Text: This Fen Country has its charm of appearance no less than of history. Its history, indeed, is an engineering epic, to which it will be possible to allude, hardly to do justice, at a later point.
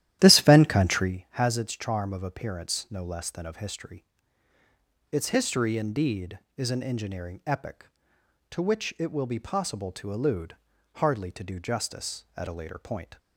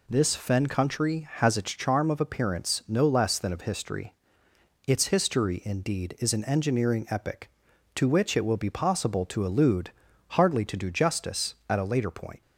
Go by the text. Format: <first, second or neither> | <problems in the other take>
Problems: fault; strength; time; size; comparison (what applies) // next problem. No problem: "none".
second | starts louder than the rest; strong; until 1.1 s; 12.5 dB